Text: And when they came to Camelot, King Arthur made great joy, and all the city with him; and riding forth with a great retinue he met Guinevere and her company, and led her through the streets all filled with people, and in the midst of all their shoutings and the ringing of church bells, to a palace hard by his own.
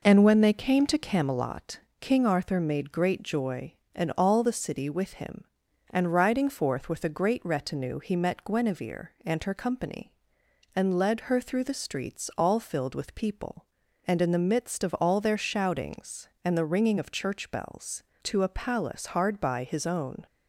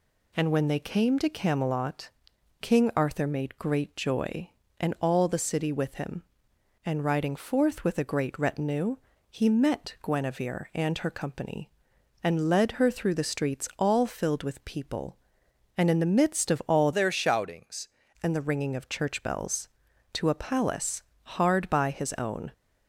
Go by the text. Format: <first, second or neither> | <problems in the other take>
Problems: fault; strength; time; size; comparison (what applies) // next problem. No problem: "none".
first | pauses between "retinue" and "he"; slight; at 8.9 s; 0.34 s long // changes voice from "their" to "shoutings"; from 16.9 to 17.8 s; 0.9 s long // pauses between "palace" and "hard"; slight; at 21.0 s; 0.22 s long